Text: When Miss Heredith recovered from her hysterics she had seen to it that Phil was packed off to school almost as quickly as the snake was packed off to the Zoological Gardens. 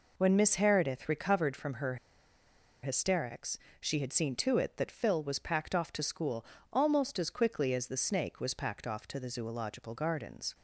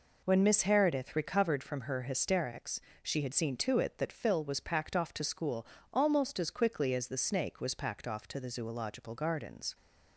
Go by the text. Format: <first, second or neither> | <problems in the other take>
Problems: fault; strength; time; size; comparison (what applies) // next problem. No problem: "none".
second | pauses between "her" and "hysterics"; noticeable; at 1.9 s; 0.87 s long // pauses between "hysterics" and "she"; slight; at 3.5 s; 0.24 s long; slight in the second // pauses between "school" and "almost"; slight; at 6.4 s; 0.30 s long; slight in the second